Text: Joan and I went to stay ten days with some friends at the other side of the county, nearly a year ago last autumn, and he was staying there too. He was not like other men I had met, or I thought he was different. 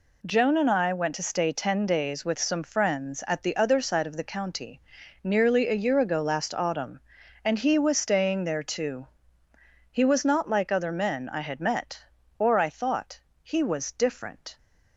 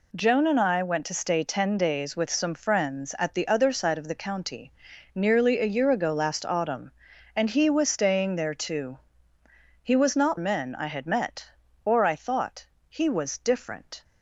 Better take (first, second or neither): first